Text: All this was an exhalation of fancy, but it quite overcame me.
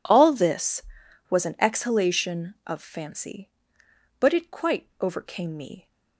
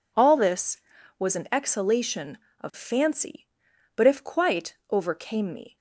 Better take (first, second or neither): first